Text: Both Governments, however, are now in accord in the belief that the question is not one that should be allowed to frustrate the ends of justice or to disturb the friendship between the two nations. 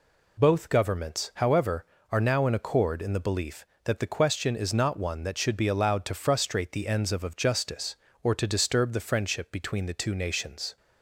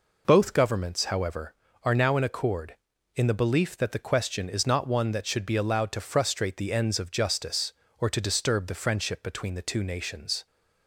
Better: second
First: says "of" twice; at 7.2 s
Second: none

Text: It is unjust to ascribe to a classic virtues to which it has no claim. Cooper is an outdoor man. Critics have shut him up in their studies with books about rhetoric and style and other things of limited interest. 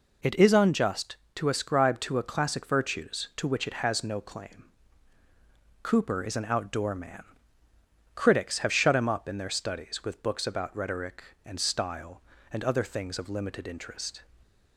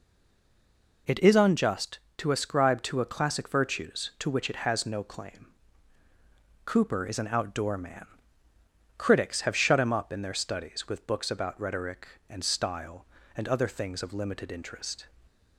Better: first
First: none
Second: stays silent before the first word; until 1.0 s; 1.0 s long

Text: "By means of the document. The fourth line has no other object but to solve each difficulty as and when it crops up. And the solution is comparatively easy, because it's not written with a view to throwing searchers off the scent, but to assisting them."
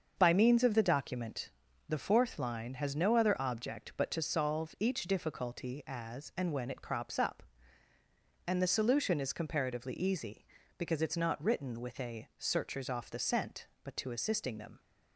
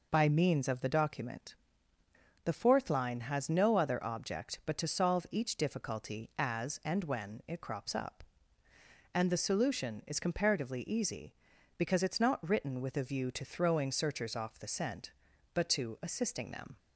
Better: second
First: starts louder than the rest; until 1.2 s; 6.5 dB // skips "view to throwing"; at 12.3 s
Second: none

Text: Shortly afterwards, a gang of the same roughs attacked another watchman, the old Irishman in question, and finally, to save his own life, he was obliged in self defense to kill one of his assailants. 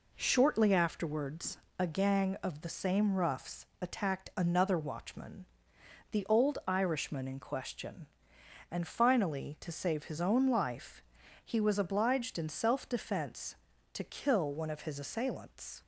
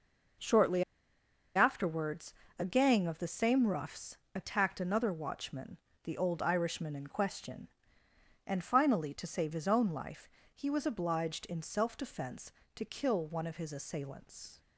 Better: first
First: pauses between "roughs" and "attacked"; slight; at 3.6 s; 0.16 s long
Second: pauses between "Shortly" and "afterwards"; noticeable; at 0.8 s; 0.72 s long // pauses between "roughs" and "attacked"; slight; at 4.1 s; 0.18 s long

